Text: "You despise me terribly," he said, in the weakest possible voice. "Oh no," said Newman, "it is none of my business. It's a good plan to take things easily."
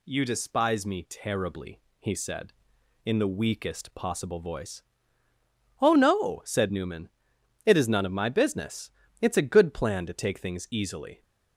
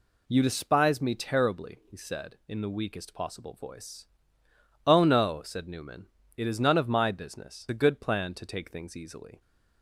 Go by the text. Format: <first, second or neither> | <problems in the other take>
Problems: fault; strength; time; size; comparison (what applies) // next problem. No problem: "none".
first | skips "It's"; at 7.6 s